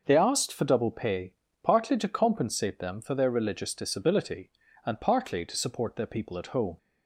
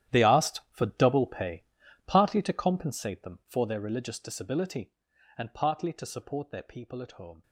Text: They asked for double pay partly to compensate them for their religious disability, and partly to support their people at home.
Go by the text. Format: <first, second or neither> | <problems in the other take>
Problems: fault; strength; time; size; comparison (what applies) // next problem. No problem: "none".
first | gets quieter; strong; throughout; 15.5 dB // pauses between "pay" and "partly"; at 1.6 s; 0.42 s long; slight in the first